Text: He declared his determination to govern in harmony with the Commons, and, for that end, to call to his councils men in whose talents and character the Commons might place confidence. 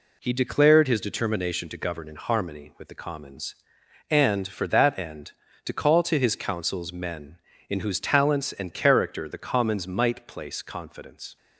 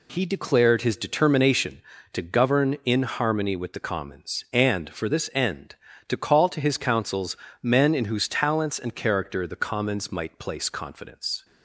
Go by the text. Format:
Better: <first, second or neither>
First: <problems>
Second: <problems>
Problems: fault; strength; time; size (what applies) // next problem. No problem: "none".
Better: first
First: none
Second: says "this" for "that"; at 5.0 s // pauses between "councils" and "men"; slight; at 7.3 s; 0.26 s long